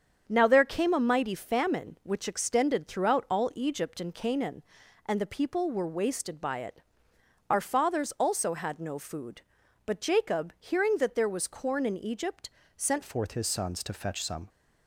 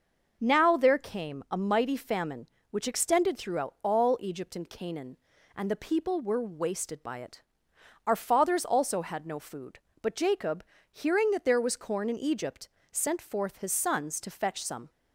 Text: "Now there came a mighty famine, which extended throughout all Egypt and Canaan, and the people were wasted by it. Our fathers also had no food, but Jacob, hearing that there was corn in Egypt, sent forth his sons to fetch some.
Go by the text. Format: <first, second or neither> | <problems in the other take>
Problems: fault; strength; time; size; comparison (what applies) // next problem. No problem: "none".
second | starts louder than the rest; strong; until 1.2 s; 7.5 dB // changes voice at "forth"; from 13.0 s on; 1.4 s long